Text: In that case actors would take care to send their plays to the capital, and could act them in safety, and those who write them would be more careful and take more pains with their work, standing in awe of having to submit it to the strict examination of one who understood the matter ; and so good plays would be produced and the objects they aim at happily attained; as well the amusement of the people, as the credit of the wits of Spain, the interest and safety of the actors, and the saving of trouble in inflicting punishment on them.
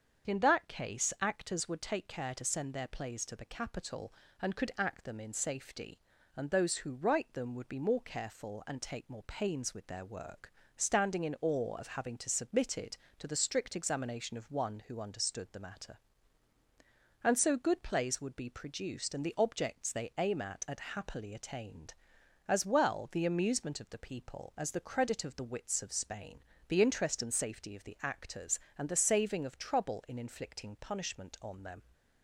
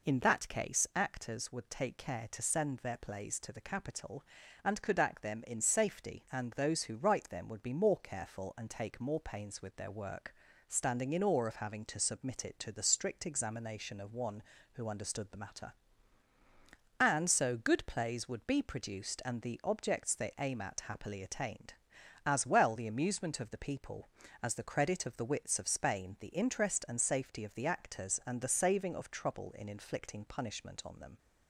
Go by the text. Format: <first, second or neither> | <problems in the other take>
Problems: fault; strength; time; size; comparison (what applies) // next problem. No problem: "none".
second | starts louder than the rest; until 1.3 s; 7 dB // says "at" twice; at 20.6 s